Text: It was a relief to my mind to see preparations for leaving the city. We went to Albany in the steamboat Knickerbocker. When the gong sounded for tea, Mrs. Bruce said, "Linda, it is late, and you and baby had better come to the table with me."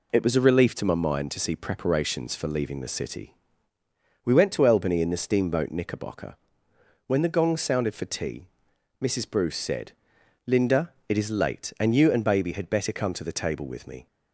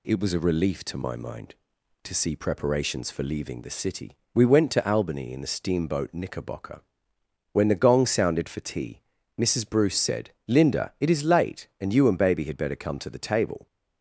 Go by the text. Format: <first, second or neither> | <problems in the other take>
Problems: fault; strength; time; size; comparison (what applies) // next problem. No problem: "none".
first | stops before "with me"; at 13.6 s